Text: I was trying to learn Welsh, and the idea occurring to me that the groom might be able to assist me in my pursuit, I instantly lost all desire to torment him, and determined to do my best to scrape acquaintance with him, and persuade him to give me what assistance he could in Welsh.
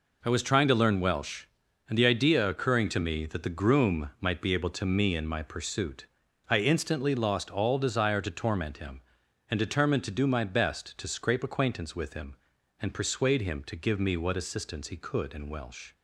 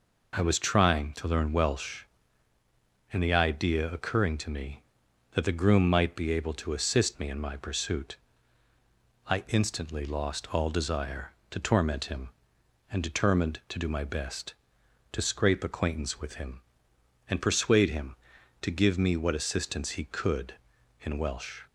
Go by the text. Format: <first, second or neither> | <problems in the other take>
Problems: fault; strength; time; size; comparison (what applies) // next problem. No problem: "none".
second | skips "assist"; at 4.8 s